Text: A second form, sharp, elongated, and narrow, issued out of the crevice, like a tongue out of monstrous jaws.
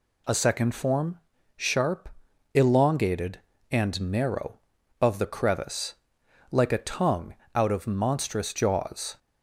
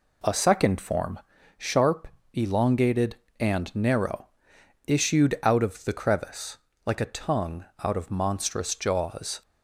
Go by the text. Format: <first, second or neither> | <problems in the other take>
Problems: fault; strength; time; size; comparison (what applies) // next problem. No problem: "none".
second | skips "issued out"; at 4.7 s // pauses between "tongue" and "out"; slight; at 7.3 s; 0.20 s long; slight in the second